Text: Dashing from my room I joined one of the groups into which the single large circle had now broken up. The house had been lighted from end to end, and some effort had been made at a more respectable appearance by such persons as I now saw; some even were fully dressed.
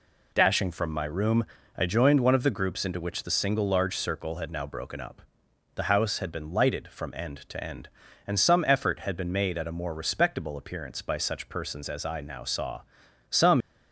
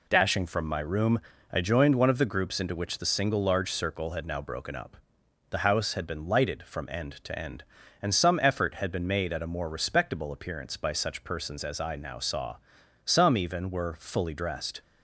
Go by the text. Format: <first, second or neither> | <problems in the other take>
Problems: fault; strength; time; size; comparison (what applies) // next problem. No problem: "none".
second | pauses between "room" and "I"; slight; at 1.4 s; 0.32 s long; slight in the second // stops before "even were fully dressed"; at 13.6 s